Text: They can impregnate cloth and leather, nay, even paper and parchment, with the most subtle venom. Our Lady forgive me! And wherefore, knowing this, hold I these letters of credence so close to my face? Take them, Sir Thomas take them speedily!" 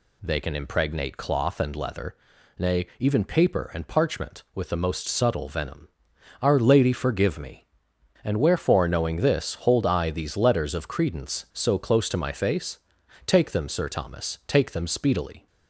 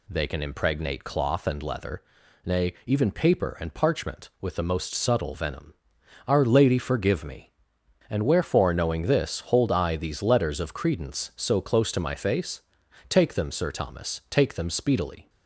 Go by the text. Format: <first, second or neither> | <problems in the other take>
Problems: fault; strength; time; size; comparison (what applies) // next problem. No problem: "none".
neither | none